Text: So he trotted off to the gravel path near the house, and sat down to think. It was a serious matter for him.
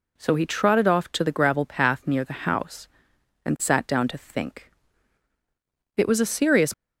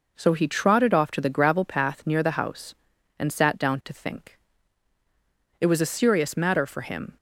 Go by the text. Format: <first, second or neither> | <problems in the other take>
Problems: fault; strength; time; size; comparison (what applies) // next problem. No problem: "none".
second | stops before "matter for him"; at 6.7 s